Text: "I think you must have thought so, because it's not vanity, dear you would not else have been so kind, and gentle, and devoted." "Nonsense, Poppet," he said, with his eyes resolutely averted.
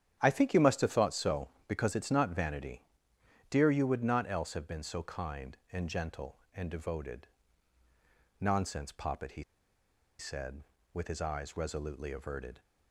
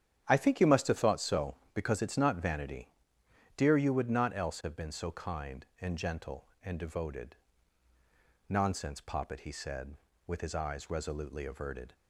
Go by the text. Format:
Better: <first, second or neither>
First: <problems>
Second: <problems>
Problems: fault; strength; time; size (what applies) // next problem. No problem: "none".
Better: second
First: starts louder than the rest; strong; until 1.2 s; 9.5 dB // pauses between "he" and "said"; noticeable; at 9.4 s; 0.75 s long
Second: starts louder than the rest; strong; until 1.2 s; 9.5 dB